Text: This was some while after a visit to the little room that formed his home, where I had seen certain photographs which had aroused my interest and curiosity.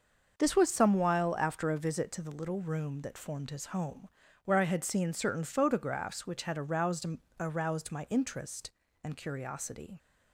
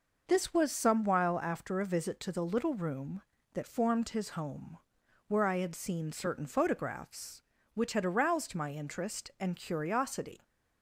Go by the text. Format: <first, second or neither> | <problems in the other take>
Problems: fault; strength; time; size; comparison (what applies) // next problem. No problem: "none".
second | starts louder than the rest; until 1.4 s; 6.5 dB // says "aroused" twice; at 7.3 s